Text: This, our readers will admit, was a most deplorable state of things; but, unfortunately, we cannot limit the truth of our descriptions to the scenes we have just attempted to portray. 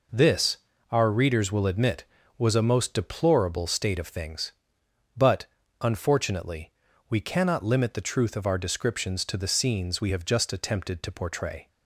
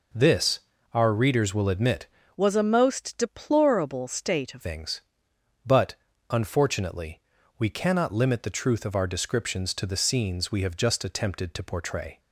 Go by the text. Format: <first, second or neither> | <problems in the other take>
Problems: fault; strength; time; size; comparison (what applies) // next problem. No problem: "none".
first | changes voice from "was" to "of"; from 2.3 to 4.6 s; 2.3 s long